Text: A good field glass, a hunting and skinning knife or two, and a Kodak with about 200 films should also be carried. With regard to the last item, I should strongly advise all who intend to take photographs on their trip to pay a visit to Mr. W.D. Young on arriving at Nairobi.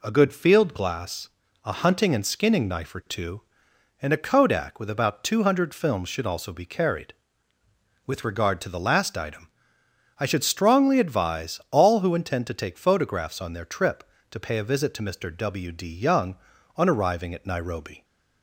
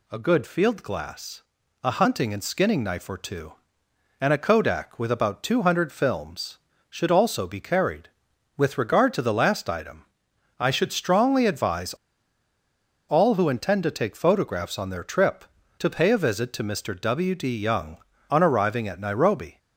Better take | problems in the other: first | pauses between "advise" and "all"; at 11.9 s; 1.1 s long

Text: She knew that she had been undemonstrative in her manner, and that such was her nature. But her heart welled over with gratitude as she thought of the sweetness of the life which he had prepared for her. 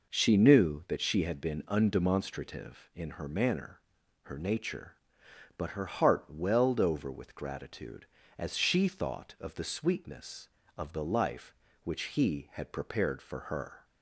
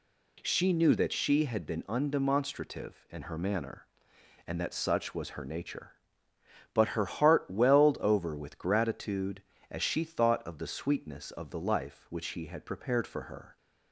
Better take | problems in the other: second | skips "and that such was"; at 4.0 s

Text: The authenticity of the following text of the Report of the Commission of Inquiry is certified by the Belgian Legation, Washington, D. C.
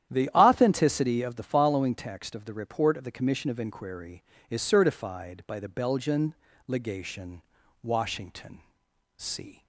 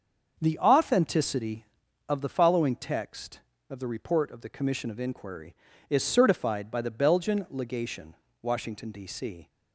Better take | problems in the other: second | starts louder than the rest; strong; until 1.1 s; 10.5 dB; also in the second // pauses between "Belgian" and "Legation"; slight; at 6.3 s; 0.32 s long // skips "D"; at 8.8 s

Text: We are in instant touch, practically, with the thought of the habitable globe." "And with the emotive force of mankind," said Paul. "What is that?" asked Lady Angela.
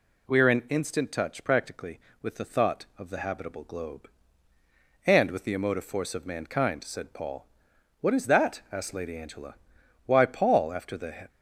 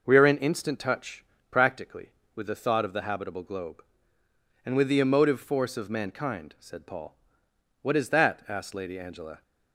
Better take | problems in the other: second | goes on to say "Why Paul after the"; noticeable; from 10.0 s on; 1.2 s long

